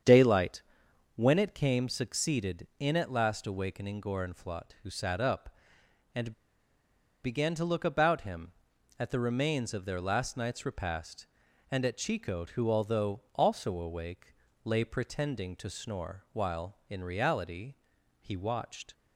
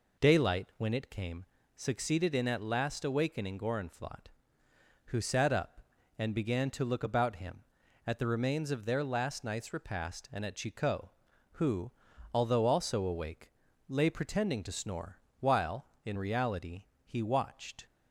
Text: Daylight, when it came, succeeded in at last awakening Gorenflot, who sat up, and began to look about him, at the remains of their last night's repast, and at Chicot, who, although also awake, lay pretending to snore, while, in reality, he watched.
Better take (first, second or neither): second